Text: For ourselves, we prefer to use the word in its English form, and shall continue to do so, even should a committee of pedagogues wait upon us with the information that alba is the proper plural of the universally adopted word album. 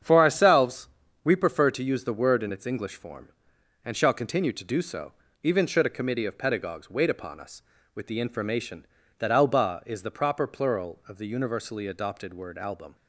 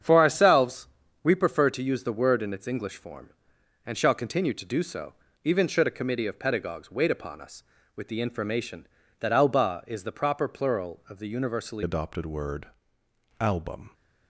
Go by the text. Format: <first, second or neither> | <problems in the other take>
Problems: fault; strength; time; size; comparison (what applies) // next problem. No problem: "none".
first | starts louder than the rest; strong; until 1.3 s; 8 dB; strong in the first // changes voice at "adopted"; from 11.8 s on; 2.1 s long // pauses between "word" and "album"; noticeable; at 12.6 s; 0.72 s long